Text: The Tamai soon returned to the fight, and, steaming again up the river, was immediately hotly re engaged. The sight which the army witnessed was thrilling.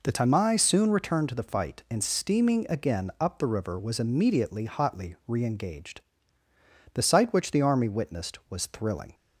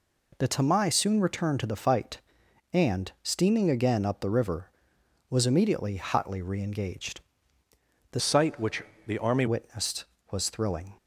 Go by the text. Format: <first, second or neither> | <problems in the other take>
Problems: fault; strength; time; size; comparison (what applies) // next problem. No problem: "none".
first | changes voice from "sight" to "army"; from 8.1 to 9.4 s; 1.3 s long // pauses between "which" and "the"; slight; at 8.8 s; 0.24 s long